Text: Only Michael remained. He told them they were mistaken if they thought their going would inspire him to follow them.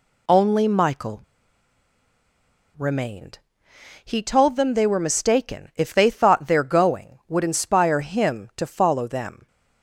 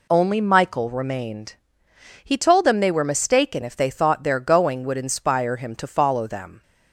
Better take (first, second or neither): second